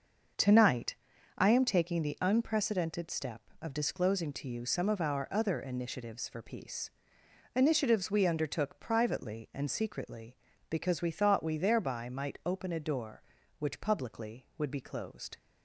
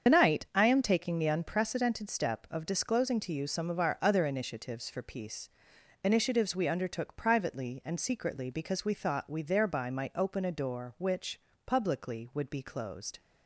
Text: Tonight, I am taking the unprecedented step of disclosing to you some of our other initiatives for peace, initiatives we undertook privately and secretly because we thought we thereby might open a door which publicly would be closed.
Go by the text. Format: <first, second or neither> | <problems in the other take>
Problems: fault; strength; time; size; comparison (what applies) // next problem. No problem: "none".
first | loses the start of "Tonight"; at 0.0 s; 100 ms // starts louder than the rest; strong; until 1.1 s; 7.5 dB; also in the first // pauses between "which" and "publicly"; slight; at 11.3 s; 0.24 s long